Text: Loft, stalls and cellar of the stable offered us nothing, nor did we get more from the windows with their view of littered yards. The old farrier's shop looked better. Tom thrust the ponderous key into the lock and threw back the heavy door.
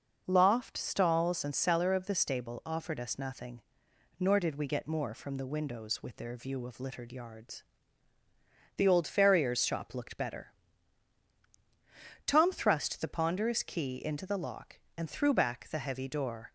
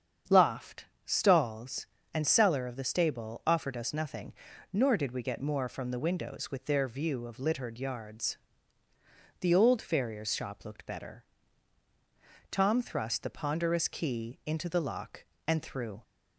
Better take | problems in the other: first | starts louder than the rest; strong; until 1.4 s; 8 dB // stops before "back the heavy door"; at 16.0 s

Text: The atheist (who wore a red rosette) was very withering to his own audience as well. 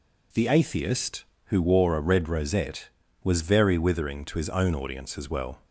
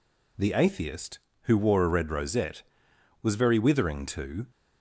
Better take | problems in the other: first | stops before "his own audience as well"; at 4.5 s

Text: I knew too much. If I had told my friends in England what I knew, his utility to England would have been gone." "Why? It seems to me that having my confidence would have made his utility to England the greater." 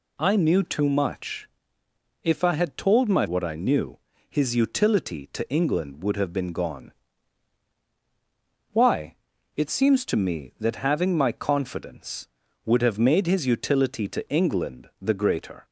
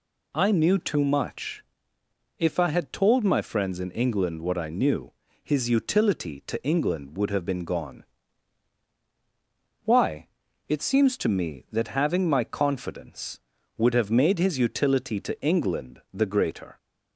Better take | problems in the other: second | skips "friends in England"; at 3.2 s

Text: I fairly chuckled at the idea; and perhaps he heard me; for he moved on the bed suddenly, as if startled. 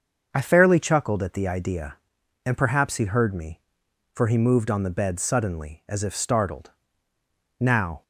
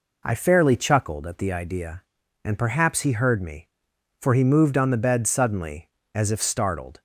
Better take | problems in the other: second | starts louder than the rest; until 1.3 s; 6.5 dB // goes on to say "Now"; slight; from 7.5 s on; 0.44 s long

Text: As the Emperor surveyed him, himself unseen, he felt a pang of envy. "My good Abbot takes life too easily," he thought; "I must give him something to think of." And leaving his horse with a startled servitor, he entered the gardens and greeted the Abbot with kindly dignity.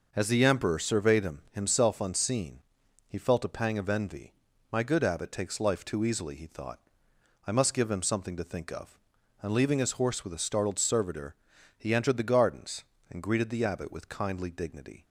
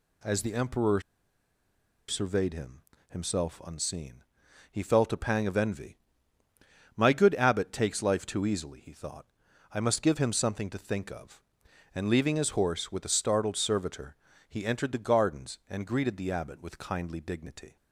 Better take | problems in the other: first | pauses between "Emperor" and "surveyed"; at 1.0 s; 1.0 s long

